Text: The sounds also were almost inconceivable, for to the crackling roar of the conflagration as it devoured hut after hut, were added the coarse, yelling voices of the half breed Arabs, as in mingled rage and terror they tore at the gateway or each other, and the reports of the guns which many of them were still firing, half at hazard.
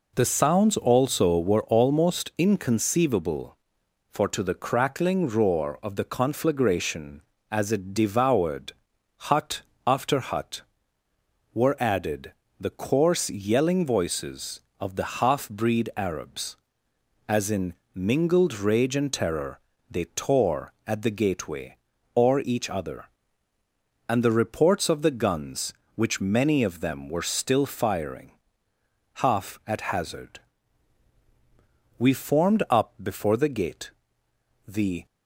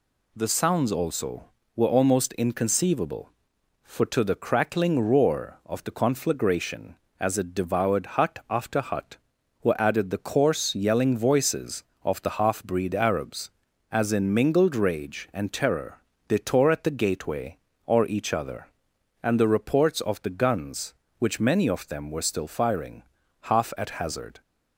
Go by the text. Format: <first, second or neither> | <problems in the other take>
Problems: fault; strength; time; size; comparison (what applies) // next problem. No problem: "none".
second | pauses between "devoured" and "hut"; noticeable; at 8.7 s; 0.56 s long // pauses between "hut" and "after"; slight; at 9.6 s; 0.26 s long // pauses between "added" and "the"; slight; at 12.3 s; 0.26 s long // pauses between "in" and "mingled"; slight; at 17.7 s; 0.22 s long // pauses between "terror" and "they"; slight; at 19.5 s; 0.30 s long; slight in the second // goes on to say "We formed up before the gate the"; strong; from 31.9 s on; 3.0 s long